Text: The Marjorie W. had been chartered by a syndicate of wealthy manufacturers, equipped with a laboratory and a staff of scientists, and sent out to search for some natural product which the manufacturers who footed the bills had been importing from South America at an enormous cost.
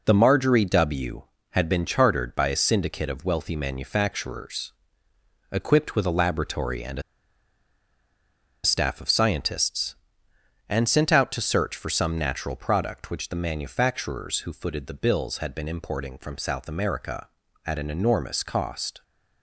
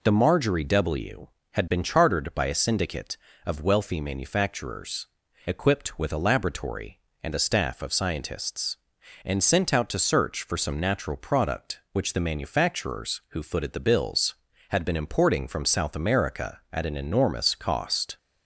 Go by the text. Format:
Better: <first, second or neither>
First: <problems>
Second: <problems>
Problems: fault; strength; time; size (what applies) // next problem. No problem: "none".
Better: second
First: pauses between "a" and "staff"; strong; at 7.0 s; 1.6 s long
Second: none